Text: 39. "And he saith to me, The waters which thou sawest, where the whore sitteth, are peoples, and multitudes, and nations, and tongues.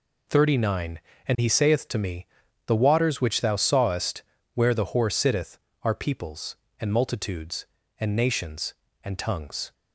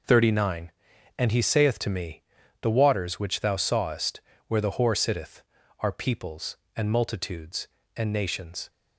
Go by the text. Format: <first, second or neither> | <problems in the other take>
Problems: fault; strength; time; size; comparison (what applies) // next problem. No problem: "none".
first | stops before "and tongues"; at 8.6 s